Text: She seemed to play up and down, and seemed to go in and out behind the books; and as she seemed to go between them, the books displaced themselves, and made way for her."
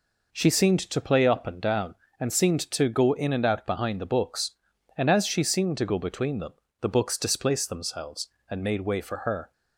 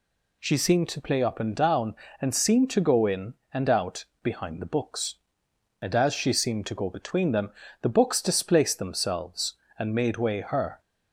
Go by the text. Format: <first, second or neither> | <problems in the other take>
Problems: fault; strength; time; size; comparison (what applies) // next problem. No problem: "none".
first | pauses between "out" and "behind"; slight; at 4.0 s; 0.18 s long // skips "for"; at 10.4 s